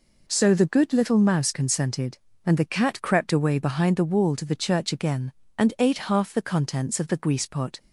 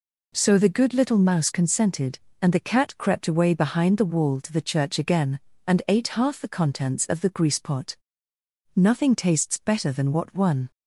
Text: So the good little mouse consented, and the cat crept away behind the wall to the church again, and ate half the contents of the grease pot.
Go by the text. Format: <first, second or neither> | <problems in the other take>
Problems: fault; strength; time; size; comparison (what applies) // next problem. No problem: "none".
first | goes on to say "Nothing tastes better than what one"; strong; from 8.7 s on; 1.9 s long